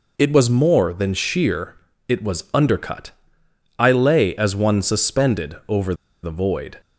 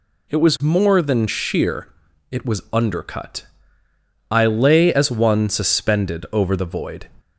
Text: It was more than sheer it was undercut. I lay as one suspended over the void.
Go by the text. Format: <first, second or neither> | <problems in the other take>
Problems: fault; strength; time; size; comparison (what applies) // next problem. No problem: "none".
second | pauses between "sheer" and "it"; slight; at 1.7 s; 0.32 s long; also in the second // pauses between "over" and "the"; slight; at 5.9 s; 0.27 s long